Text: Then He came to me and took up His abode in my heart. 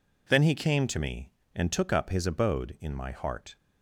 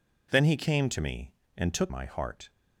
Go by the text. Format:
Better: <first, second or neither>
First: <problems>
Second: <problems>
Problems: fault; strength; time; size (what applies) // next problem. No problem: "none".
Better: first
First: none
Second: skips "up His abode in"; at 1.9 s